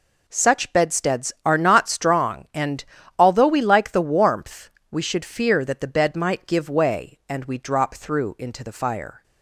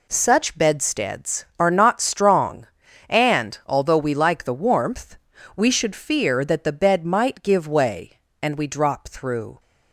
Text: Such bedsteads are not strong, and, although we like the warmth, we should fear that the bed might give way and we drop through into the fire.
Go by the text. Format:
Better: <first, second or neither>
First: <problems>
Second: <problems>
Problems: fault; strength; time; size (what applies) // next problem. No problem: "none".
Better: first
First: none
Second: stops before "into the fire"; at 9.5 s